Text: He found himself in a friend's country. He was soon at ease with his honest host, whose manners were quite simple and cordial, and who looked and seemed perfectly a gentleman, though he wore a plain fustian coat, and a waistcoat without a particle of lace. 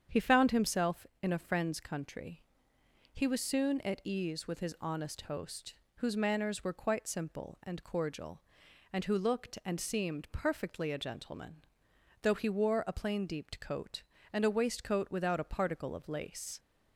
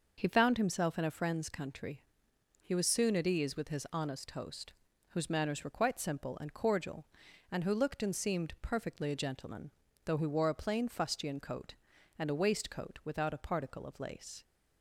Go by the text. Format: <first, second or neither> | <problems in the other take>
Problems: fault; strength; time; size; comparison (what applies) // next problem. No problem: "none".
second | starts louder than the rest; strong; until 1.2 s; 8 dB // says "deeped" for "fustian"; at 13.2 s